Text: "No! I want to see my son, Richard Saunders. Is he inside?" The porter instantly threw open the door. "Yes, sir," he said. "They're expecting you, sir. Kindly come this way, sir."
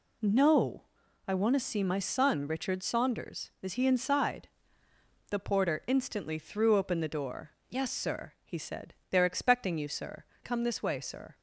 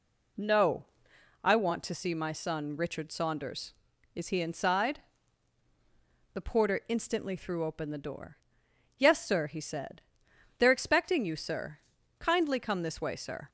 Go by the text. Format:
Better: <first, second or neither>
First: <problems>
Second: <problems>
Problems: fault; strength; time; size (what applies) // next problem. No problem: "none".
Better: second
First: skips "Kindly"; at 10.3 s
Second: none